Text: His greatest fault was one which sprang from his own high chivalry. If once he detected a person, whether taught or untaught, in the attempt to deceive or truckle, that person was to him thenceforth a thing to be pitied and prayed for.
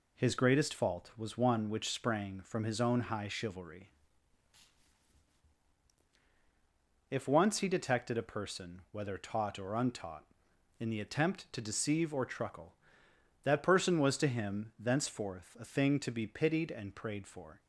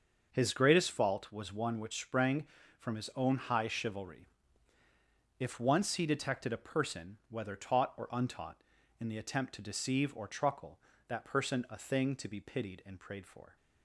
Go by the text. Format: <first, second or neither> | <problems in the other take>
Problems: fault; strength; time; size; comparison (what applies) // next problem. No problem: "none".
first | starts louder than the rest; until 1.3 s; 6.5 dB // skips "was to him thenceforth"; at 11.6 s